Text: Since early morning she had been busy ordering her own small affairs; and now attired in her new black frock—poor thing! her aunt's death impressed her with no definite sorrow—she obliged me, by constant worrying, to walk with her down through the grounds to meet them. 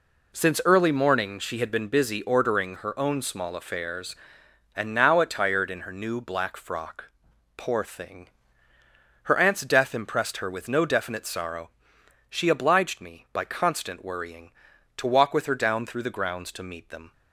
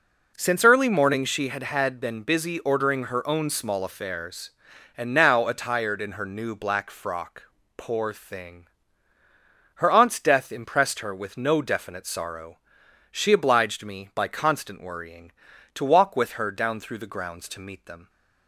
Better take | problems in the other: first | says "had" twice; at 1.6 s

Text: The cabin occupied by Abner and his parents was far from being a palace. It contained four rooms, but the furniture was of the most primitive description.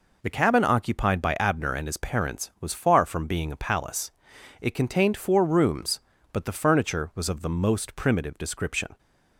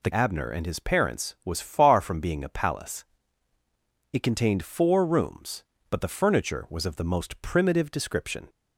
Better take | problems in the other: first | skips "cabin occupied by"; at 0.1 s

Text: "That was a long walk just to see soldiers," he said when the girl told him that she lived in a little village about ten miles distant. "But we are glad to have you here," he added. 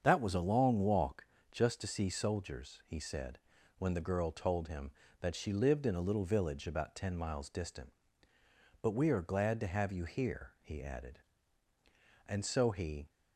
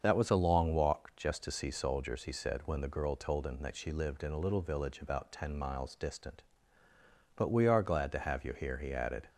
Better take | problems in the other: second | starts louder than the rest; strong; until 1.0 s; 7 dB; also in the second // pauses between "walk" and "just"; slight; at 1.2 s; 0.24 s long // pauses between "said" and "when"; at 3.4 s; 0.38 s long // goes on to say "And so he"; noticeable; from 12.2 s on; 0.80 s long

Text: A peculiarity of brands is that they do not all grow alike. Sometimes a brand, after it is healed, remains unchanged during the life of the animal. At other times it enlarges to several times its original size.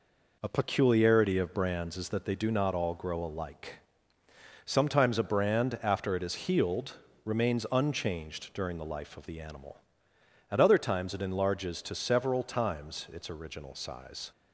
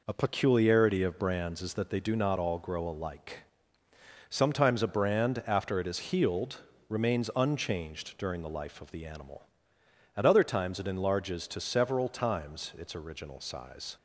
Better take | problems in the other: neither | none

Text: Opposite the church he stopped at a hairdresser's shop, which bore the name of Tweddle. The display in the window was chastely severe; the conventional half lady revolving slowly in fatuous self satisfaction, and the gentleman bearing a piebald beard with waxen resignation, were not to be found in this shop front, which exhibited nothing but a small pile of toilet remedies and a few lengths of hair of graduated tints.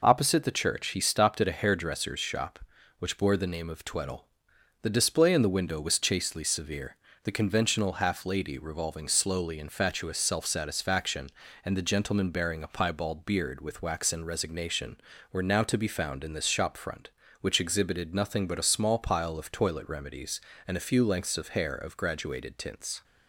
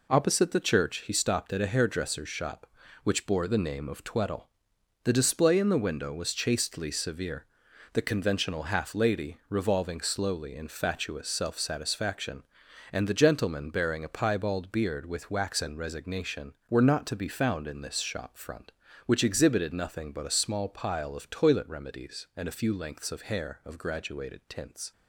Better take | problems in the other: second | says "now" for "not"; at 15.4 s

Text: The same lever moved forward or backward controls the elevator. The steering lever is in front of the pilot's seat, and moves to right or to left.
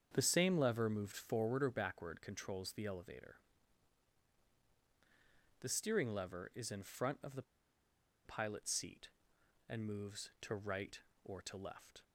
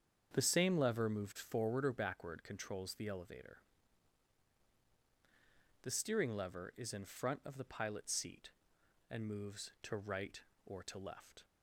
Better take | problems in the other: second | starts louder than the rest; strong; until 1.1 s; 7.5 dB; strong in the second // pauses between "the" and "pilot's"; noticeable; at 7.4 s; 0.82 s long

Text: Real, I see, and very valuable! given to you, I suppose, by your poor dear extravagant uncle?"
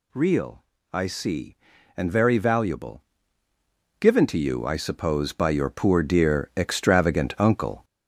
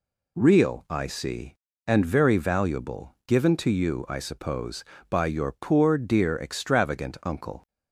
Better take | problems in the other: second | gets louder; noticeable; throughout; 5.5 dB

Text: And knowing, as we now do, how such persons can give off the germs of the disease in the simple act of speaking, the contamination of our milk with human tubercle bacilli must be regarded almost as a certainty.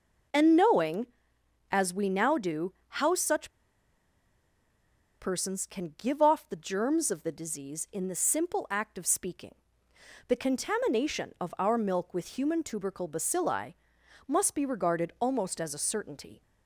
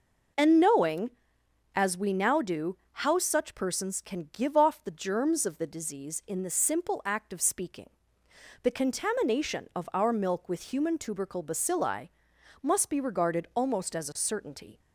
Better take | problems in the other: second | pauses between "such" and "persons"; strong; at 3.5 s; 1.6 s long // pauses between "bacilli" and "must"; noticeable; at 13.7 s; 0.54 s long; noticeable in the second

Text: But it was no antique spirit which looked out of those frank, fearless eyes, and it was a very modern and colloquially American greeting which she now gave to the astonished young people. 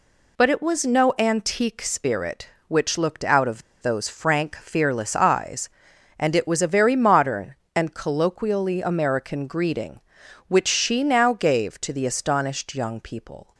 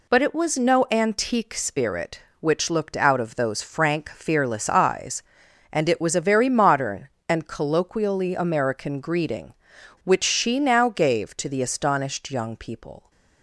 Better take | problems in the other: second | pauses between "of" and "those"; slight; at 3.6 s; 0.20 s long

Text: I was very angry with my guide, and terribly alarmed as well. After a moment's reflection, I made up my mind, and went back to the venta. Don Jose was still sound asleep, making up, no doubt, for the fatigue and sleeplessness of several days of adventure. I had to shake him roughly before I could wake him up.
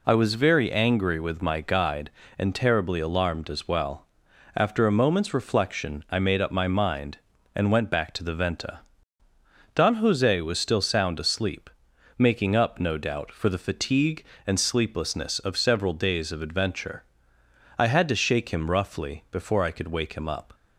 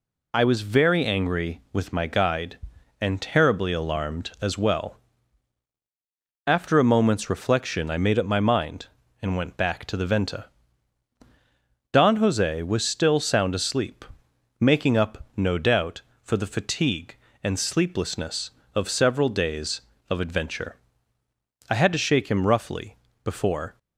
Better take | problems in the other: first | pauses between "roughly" and "before"; slight; at 22.9 s; 0.28 s long // stops before "I could wake him up"; at 23.7 s

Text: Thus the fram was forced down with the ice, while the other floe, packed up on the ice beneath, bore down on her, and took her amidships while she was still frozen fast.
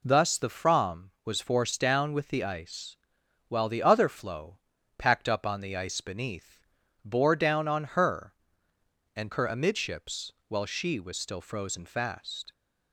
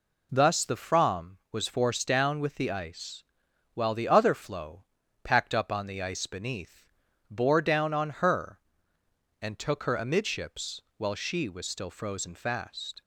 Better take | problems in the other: second | skips "took"; at 9.3 s // pauses between "amidships" and "while"; slight; at 10.3 s; 0.16 s long; slight in the second

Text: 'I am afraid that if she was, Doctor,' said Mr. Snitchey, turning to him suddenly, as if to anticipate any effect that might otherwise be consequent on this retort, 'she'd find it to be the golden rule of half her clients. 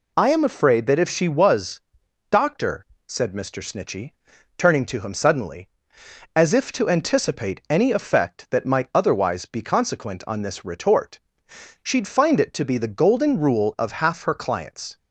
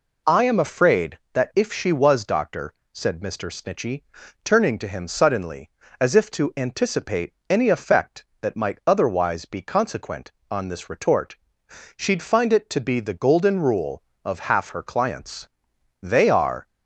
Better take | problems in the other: first | pauses between "anticipate" and "any"; slight; at 7.3 s; 0.16 s long // goes on to say "They are"; noticeable; from 16.0 s on; 0.64 s long

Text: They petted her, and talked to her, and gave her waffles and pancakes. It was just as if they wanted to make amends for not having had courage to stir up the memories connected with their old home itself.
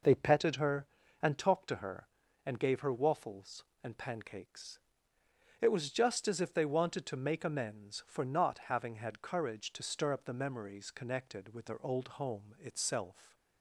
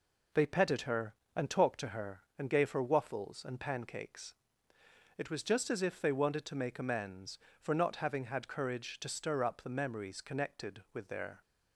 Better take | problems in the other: first | stops before "old home itself"; at 11.4 s

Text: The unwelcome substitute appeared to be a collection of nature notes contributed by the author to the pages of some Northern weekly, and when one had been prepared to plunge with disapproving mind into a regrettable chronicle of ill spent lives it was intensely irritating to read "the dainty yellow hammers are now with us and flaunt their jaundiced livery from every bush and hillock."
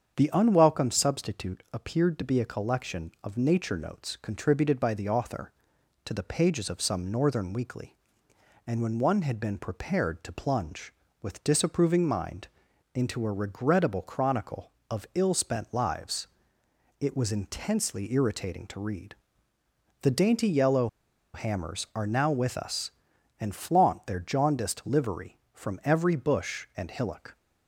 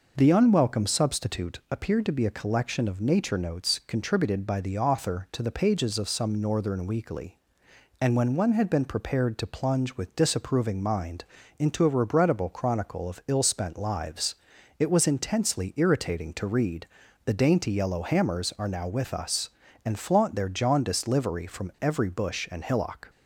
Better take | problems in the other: second | starts louder than the rest; strong; until 1.1 s; 7.5 dB // pauses between "mind" and "into"; noticeable; at 12.4 s; 0.48 s long; slight in the second // pauses between "lives" and "it"; noticeable; at 16.2 s; 0.72 s long; also in the second // pauses between "read" and "the"; noticeable; at 19.1 s; 0.88 s long; also in the second // pauses between "yellow" and "hammers"; noticeable; at 20.8 s; 0.47 s long

